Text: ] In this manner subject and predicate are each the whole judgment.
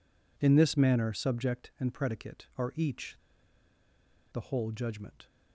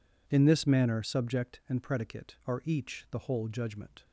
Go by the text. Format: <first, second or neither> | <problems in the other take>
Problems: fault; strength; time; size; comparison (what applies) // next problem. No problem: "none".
second | pauses between "each" and "the"; at 3.1 s; 1.1 s long